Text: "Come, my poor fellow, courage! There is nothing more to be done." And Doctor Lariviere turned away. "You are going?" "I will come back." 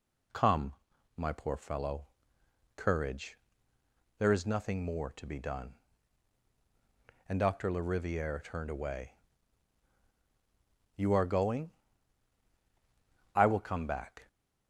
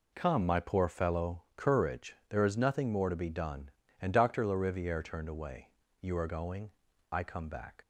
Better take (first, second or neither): first